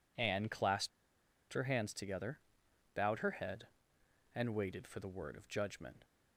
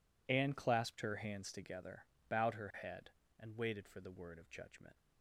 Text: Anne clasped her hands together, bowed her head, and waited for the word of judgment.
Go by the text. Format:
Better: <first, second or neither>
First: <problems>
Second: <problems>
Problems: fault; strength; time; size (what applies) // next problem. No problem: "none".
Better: second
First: pauses between "clasped" and "her"; noticeable; at 0.8 s; 0.62 s long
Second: none